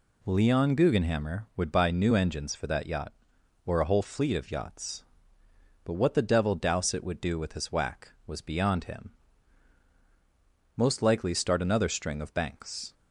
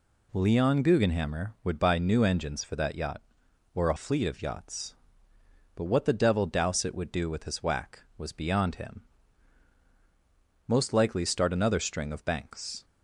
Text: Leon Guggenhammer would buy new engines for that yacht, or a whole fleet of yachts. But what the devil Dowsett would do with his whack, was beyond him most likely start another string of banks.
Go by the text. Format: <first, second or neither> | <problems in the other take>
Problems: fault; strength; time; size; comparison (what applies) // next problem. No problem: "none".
first | skips "whole"; at 3.9 s // pauses between "him" and "most"; strong; at 9.0 s; 1.6 s long; strong in the first